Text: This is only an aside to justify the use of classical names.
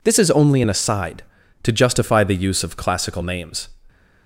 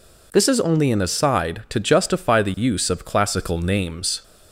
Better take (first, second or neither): neither